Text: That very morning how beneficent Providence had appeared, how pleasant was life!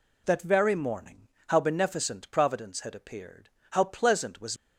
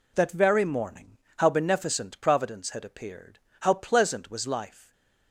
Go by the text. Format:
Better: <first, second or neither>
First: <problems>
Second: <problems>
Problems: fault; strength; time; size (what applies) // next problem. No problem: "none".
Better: second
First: pauses between "morning" and "how"; slight; at 1.2 s; 0.20 s long // stops before "life"; at 4.5 s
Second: pauses between "morning" and "how"; slight; at 1.1 s; 0.20 s long